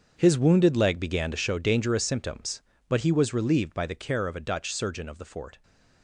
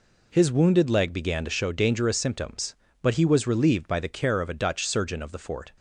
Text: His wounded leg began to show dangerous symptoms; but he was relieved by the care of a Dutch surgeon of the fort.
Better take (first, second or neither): second